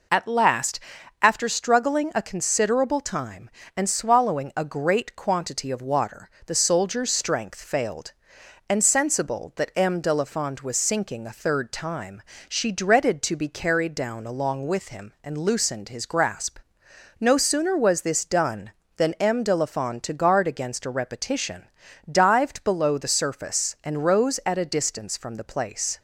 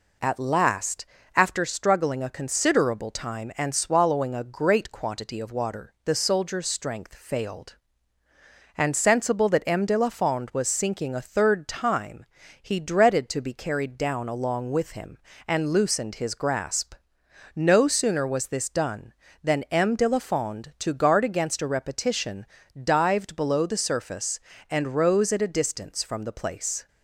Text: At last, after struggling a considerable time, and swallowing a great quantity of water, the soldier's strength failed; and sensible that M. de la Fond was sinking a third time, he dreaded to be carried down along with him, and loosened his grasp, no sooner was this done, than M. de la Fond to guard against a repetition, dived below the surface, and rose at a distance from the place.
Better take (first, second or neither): second